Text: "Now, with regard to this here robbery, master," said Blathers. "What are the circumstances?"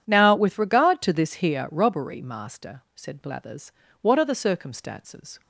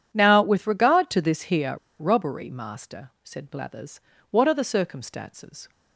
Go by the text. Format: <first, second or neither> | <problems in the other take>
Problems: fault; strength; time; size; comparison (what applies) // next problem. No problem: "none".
first | pauses between "here" and "robbery"; slight; at 1.7 s; 0.24 s long